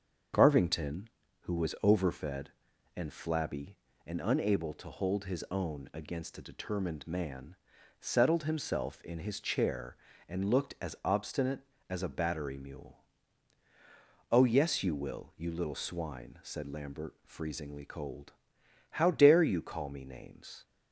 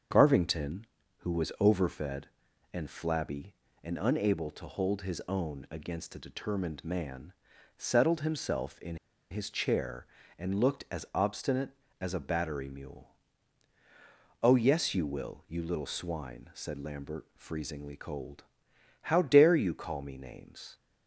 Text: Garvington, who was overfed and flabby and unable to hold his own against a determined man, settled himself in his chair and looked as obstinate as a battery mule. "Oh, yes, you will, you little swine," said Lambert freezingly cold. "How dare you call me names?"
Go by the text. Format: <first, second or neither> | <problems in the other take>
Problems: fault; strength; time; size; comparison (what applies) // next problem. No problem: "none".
first | starts louder than the rest; until 1.4 s; 7 dB; also in the first // pauses between "in" and "his"; slight; at 8.9 s; 0.34 s long